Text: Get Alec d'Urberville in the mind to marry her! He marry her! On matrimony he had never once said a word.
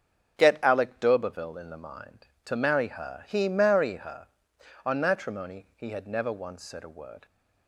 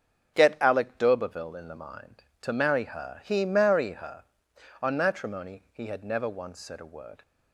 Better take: neither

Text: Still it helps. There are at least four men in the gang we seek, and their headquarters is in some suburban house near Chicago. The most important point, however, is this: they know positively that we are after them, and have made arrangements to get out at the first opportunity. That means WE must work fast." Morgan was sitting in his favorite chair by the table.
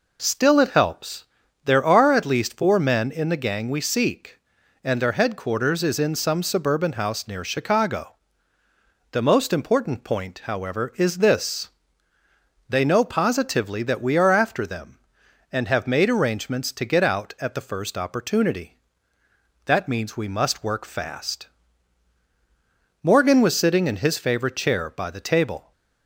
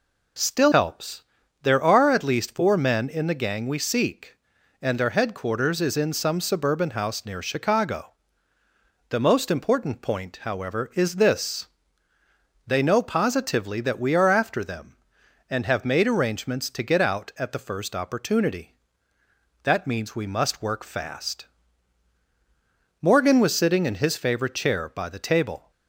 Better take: first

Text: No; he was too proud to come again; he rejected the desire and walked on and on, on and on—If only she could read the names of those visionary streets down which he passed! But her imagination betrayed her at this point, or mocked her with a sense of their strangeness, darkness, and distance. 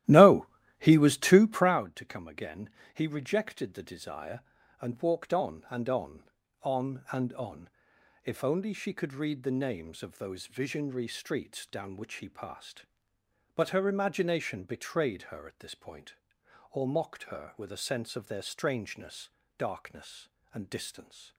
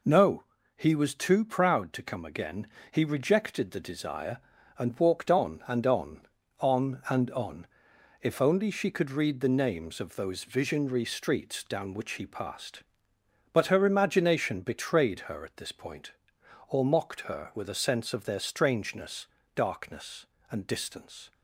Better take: second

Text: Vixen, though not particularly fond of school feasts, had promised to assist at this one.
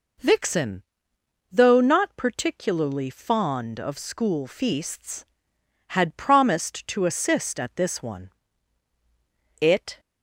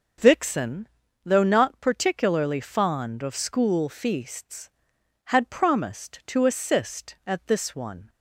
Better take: second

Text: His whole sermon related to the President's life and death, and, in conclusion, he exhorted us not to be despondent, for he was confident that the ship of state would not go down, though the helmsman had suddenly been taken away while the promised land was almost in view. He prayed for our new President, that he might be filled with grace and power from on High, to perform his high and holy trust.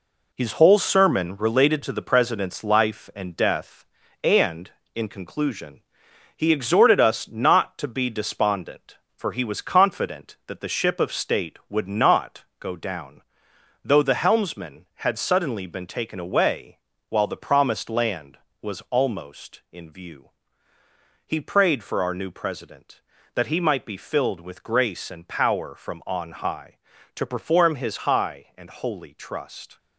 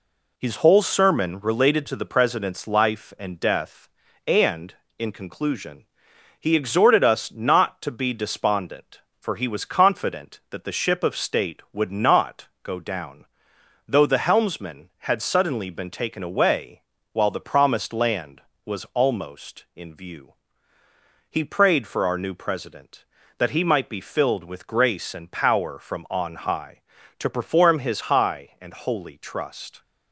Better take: second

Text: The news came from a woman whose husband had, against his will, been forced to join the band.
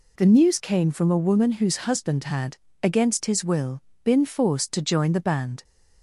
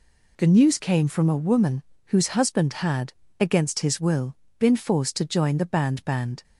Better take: first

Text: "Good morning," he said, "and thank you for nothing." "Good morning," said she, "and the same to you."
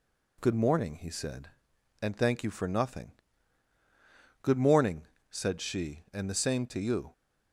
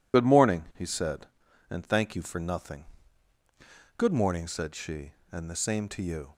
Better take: first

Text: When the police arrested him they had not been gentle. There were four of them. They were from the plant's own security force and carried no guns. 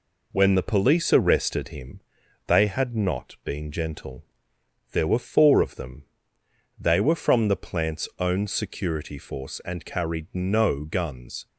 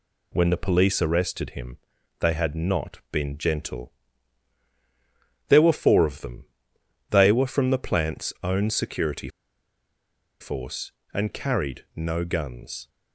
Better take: first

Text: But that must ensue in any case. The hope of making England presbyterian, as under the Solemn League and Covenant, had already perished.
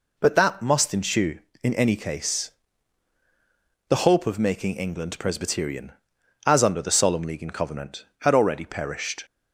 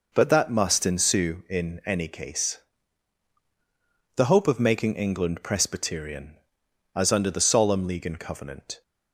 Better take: first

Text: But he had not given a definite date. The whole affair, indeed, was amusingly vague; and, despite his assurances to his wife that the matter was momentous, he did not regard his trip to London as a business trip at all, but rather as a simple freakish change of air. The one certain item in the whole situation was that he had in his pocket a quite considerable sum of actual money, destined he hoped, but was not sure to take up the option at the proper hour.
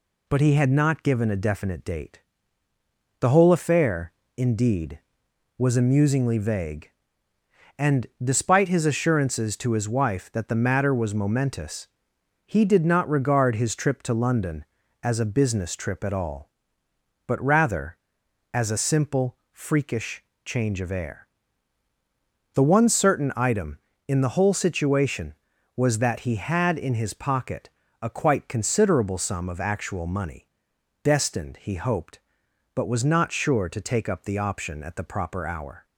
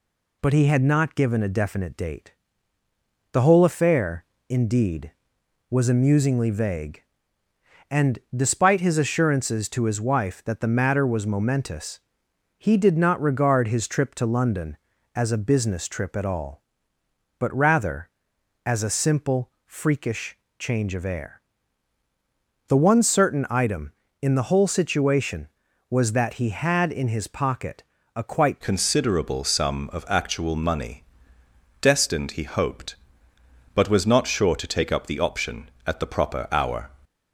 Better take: first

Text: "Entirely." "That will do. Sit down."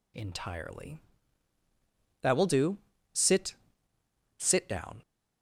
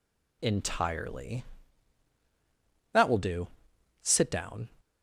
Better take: second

